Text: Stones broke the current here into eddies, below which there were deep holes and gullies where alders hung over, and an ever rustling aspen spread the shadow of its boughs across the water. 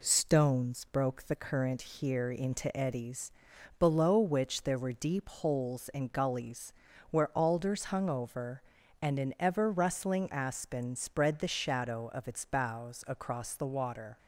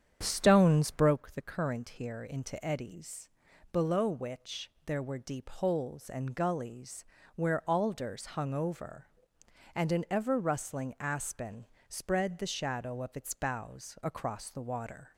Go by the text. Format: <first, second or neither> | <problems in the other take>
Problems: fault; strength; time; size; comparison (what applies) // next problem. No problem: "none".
first | starts louder than the rest; strong; until 1.2 s; 8.5 dB // pauses between "which" and "there"; slight; at 4.6 s; 0.16 s long // pauses between "gullies" and "where"; slight; at 7.0 s; 0.30 s long; also in the first // pauses between "aspen" and "spread"; slight; at 11.6 s; 0.24 s long